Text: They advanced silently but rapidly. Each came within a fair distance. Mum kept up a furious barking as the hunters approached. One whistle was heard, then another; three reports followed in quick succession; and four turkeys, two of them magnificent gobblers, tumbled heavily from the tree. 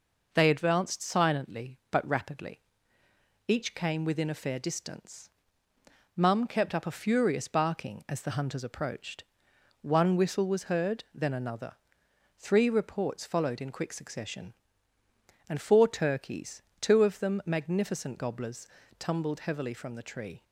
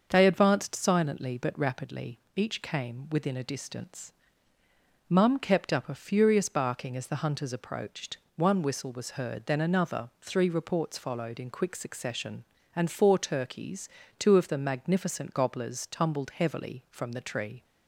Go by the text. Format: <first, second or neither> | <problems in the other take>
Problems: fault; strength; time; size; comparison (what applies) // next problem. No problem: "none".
first | starts louder than the rest; until 1.1 s; 6.5 dB // skips "fair"; at 3.4 s